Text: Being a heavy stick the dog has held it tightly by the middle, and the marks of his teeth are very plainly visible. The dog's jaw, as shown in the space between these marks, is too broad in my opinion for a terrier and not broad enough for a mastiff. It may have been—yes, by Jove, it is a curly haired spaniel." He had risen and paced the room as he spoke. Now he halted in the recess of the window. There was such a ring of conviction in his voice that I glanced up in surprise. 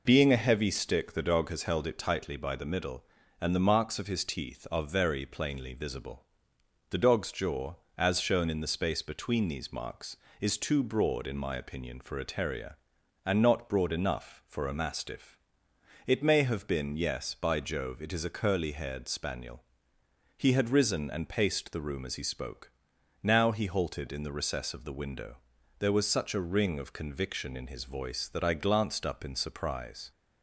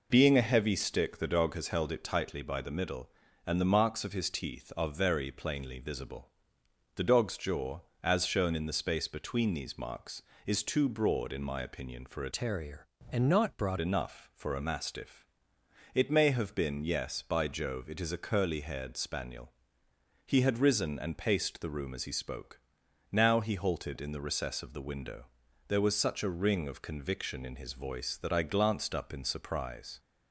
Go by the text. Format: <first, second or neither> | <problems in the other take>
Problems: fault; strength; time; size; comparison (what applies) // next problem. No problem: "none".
first | changes voice from "terrier" to "broad"; from 12.3 to 13.7 s; 1.4 s long